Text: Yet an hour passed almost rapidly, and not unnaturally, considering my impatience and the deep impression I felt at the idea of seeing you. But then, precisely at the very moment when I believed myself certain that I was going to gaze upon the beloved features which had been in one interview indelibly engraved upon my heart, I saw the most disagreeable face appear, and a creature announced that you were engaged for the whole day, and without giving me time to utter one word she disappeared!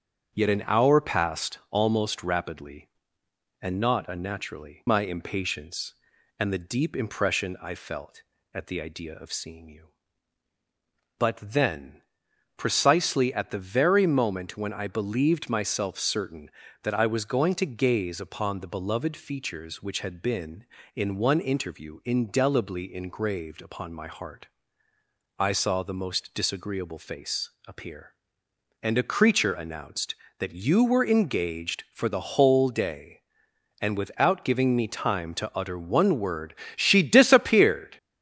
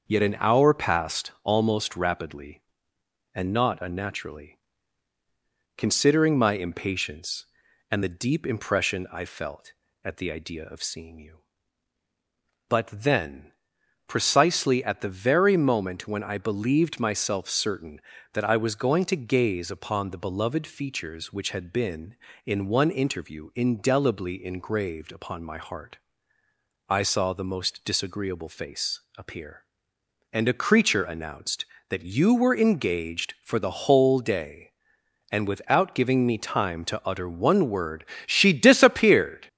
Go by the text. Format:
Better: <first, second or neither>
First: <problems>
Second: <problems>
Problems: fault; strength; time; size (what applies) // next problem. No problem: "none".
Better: second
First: starts louder than the rest; strong; until 1.3 s; 7.5 dB // skips "considering"; at 4.8 s // pauses between "face" and "appear"; slight; at 27.5 s; 0.16 s long // pauses between "word" and "she"; slight; at 36.5 s; 0.22 s long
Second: starts louder than the rest; until 1.0 s; 6.5 dB // pauses between "face" and "appear"; slight; at 29.0 s; 0.16 s long // pauses between "word" and "she"; slight; at 38.0 s; 0.22 s long